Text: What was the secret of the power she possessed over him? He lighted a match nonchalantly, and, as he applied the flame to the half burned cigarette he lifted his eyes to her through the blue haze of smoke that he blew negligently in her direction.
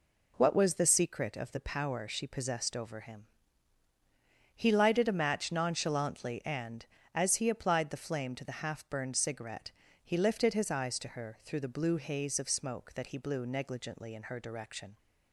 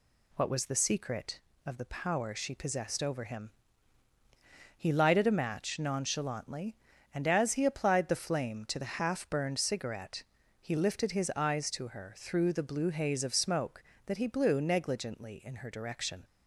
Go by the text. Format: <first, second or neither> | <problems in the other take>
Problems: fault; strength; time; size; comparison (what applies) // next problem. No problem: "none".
neither | pauses between "cigarette" and "he"; the same in both